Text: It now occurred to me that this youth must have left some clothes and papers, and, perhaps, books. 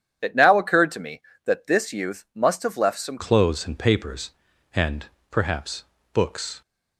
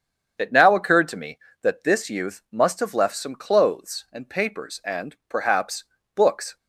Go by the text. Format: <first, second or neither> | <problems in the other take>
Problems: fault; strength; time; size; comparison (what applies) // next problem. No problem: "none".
second | starts louder than the rest; strong; until 1.2 s; 9 dB; strong in the second // changes voice at "clothes"; from 3.1 s on; 3.5 s long